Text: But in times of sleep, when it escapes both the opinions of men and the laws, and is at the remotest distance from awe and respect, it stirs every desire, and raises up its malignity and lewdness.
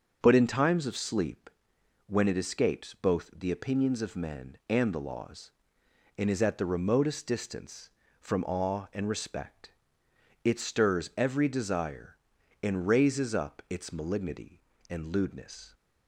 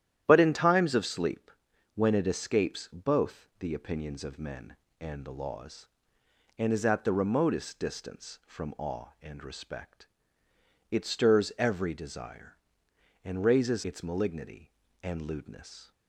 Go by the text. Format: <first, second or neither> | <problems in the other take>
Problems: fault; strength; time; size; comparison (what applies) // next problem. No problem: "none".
first | starts louder than the rest; strong; until 1.2 s; 11.5 dB; also in the first // skips "up"; at 13.8 s